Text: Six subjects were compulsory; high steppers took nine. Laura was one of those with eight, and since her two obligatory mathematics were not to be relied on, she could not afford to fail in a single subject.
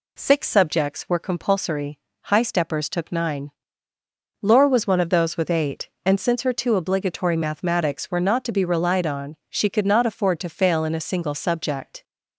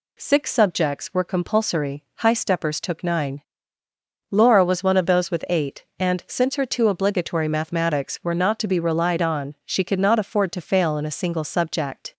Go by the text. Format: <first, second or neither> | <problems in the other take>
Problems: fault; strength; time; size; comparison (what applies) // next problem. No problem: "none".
neither | none